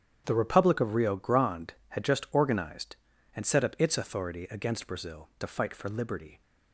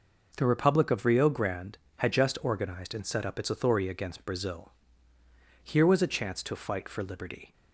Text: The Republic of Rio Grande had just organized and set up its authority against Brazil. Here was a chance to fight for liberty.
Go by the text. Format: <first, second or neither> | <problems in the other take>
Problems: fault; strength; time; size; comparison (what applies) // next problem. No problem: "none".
second | starts louder than the rest; strong; until 1.2 s; 9 dB // skips "Here was a chance"; at 5.3 s